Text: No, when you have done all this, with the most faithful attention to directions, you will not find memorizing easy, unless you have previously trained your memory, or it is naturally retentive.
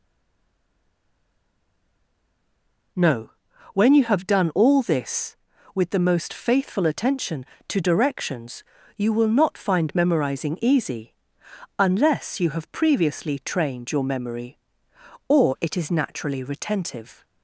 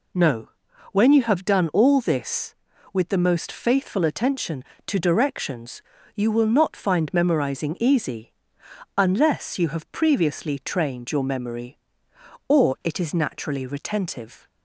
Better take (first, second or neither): second